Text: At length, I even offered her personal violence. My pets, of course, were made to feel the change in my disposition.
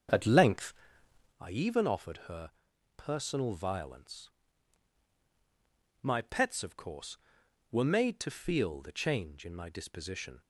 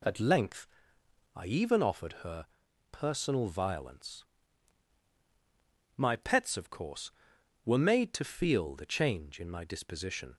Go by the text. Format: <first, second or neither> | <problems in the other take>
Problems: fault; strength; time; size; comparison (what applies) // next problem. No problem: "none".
second | starts louder than the rest; until 1.4 s; 7 dB // pauses between "her" and "personal"; at 2.5 s; 0.44 s long; also in the second